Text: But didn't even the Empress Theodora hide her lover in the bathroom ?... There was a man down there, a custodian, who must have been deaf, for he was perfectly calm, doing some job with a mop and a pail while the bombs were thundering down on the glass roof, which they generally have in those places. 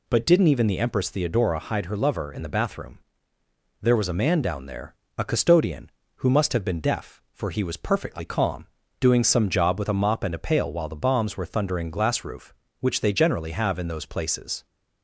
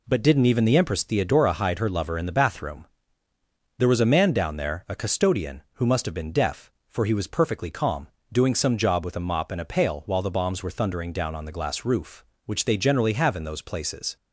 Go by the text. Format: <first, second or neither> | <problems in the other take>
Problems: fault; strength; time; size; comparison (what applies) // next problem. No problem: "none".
second | skips "down on the"; at 11.9 s